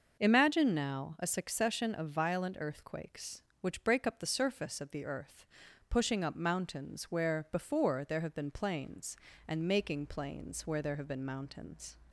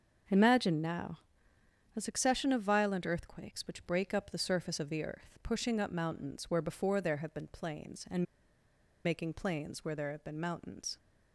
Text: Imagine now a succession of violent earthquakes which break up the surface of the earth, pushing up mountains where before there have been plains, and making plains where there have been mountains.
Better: first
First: none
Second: starts louder than the rest; until 2.0 s; 6.5 dB // pauses between "now" and "a"; noticeable; at 1.1 s; 0.76 s long // pauses between "and" and "making"; noticeable; at 8.2 s; 0.79 s long

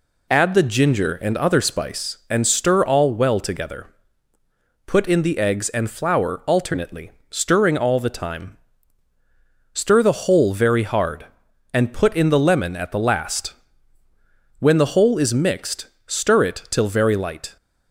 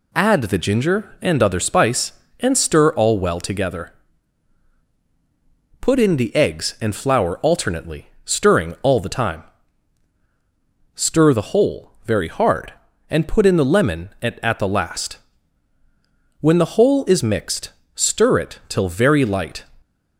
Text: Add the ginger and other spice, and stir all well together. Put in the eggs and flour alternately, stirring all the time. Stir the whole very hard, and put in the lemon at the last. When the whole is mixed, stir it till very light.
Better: first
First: none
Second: says "at" twice; at 14.4 s

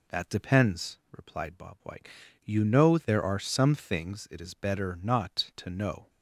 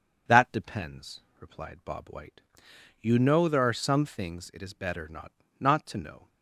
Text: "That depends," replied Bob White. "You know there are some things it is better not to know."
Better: first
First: none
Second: says "not" twice; at 5.5 s

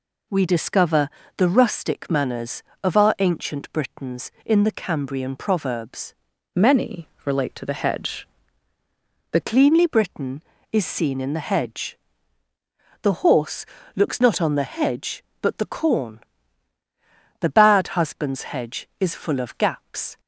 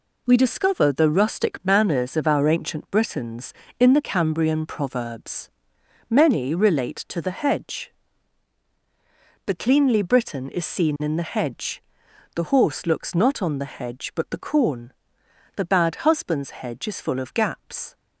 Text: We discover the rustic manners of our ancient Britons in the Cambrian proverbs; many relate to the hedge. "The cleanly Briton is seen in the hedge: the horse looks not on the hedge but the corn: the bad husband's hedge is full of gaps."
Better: second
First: pauses between "discover" and "the"; slight; at 1.0 s; 0.28 s long // changes voice from "many" to "The"; from 6.5 to 9.4 s; 2.9 s long // pauses between "many" and "relate"; slight; at 7.1 s; 0.16 s long // pauses between "horse" and "looks"; slight; at 13.6 s; 0.32 s long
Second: none

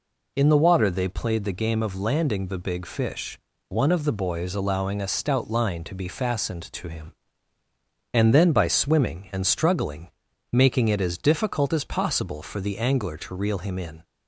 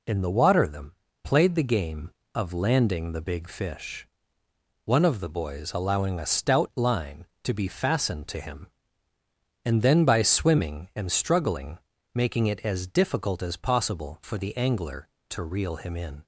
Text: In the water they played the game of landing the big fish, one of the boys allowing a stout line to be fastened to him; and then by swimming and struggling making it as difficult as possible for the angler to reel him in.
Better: first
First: pauses between "struggling" and "making"; at 10.0 s; 0.44 s long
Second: says "them" for "they"; at 0.6 s // pauses between "struggling" and "making"; slight; at 11.7 s; 0.36 s long

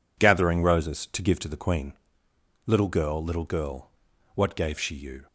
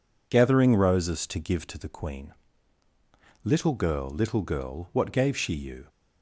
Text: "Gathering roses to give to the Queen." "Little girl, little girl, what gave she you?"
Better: neither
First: none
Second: none

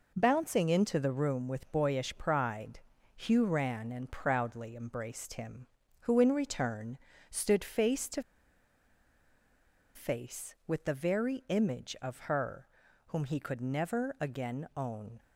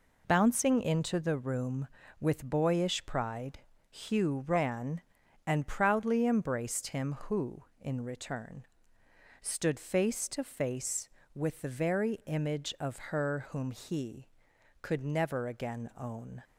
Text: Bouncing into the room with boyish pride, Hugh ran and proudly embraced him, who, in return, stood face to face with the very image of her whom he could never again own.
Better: second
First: pauses between "to" and "face"; strong; at 8.2 s; 1.7 s long // pauses between "her" and "whom"; at 12.6 s; 0.40 s long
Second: none

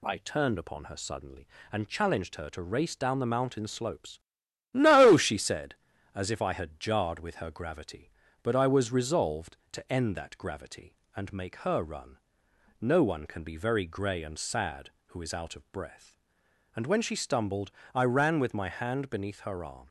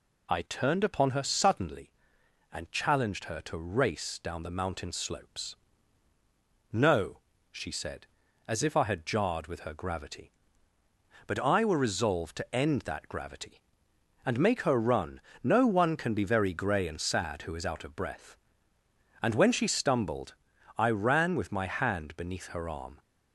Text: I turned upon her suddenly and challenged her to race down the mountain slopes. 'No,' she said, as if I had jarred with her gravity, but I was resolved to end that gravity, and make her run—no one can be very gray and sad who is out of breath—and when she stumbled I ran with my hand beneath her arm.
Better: first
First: pauses between "stumbled" and "I"; slight; at 17.7 s; 0.22 s long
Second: says "were" for "was"; at 11.6 s // pauses between "stumbled" and "I"; at 20.3 s; 0.44 s long

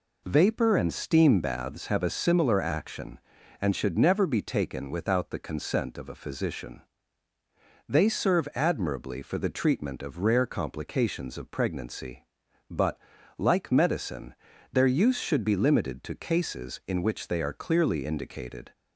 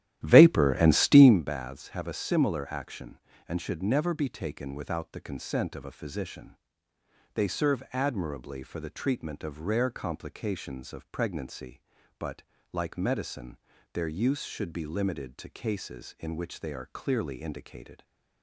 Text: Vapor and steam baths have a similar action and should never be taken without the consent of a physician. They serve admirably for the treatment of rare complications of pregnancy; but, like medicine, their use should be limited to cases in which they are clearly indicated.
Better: first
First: none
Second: starts louder than the rest; strong; until 1.4 s; 12.5 dB

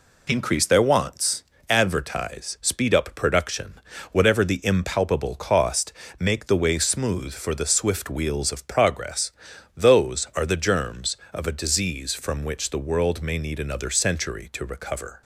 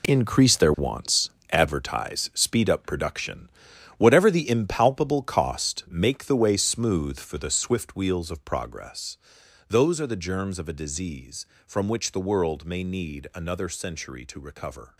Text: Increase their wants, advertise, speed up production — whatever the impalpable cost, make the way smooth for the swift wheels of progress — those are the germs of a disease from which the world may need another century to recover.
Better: first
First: none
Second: gets quieter; strong; throughout; 11 dB

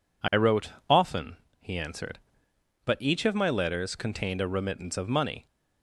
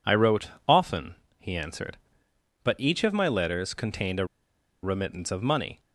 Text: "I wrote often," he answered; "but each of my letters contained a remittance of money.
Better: first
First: pauses between "wrote" and "often"; slight; at 0.7 s; 0.18 s long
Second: pauses between "wrote" and "often"; slight; at 0.4 s; 0.18 s long // pauses between "a" and "remittance"; noticeable; at 4.2 s; 0.57 s long

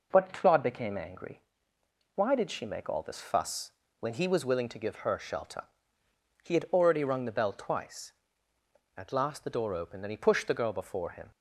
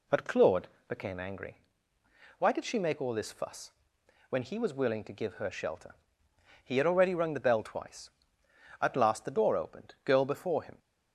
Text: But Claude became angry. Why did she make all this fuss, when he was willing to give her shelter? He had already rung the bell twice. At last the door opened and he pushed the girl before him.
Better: first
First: none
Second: pauses between "Claude" and "became"; slight; at 0.6 s; 0.20 s long // skips "and he pushed the"; at 9.9 s

